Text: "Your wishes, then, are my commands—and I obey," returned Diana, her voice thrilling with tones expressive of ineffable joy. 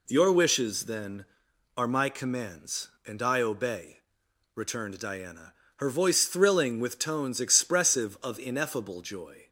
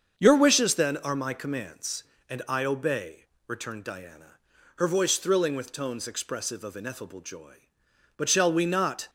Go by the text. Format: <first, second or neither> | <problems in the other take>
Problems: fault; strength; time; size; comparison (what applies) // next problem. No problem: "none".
first | starts louder than the rest; until 1.2 s; 7 dB // goes on to say "But shall we not"; noticeable; from 8.1 s on; 0.92 s long